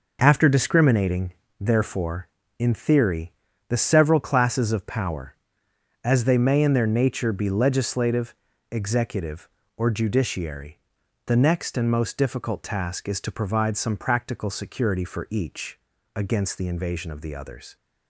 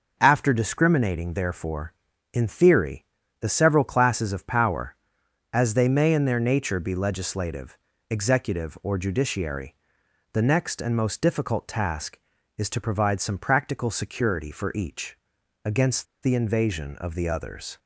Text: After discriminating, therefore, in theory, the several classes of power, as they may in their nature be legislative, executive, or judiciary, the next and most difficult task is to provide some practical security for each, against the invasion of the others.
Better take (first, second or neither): first